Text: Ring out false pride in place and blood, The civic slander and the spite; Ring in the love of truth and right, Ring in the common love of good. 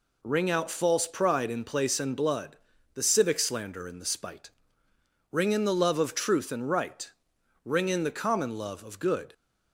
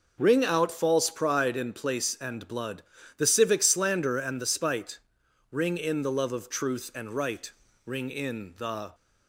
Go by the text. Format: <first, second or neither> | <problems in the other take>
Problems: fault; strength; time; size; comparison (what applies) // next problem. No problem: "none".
first | stops before "common love of good"; at 8.9 s